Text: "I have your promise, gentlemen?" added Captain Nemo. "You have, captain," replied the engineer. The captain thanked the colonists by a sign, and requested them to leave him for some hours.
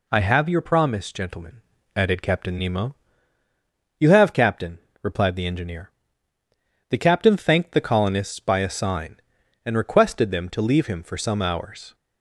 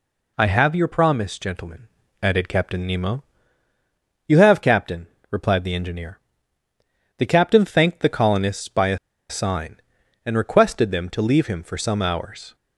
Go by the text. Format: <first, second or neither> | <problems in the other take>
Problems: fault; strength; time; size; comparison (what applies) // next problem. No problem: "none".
first | pauses between "a" and "sign"; slight; at 8.9 s; 0.32 s long